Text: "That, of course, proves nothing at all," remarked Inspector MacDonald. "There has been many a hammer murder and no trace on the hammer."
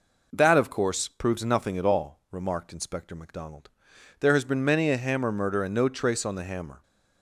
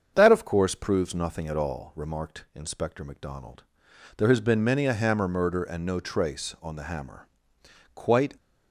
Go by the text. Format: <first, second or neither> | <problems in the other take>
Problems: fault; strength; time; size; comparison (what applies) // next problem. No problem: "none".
first | starts louder than the rest; until 1.1 s; 7 dB // goes on to say "Quite"; slight; from 7.9 s on; 0.40 s long